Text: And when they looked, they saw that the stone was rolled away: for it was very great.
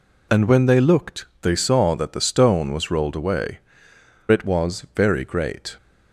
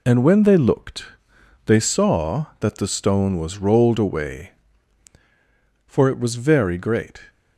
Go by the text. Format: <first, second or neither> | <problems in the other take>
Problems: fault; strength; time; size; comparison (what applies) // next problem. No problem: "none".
second | skips "for"; at 3.9 s